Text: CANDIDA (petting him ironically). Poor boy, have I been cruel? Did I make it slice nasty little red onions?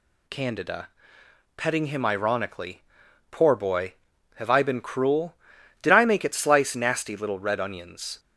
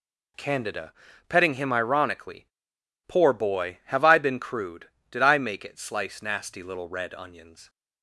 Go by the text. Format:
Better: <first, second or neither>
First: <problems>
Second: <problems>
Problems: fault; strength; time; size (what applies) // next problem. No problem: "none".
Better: first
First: none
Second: says "crude" for "cruel"; at 4.4 s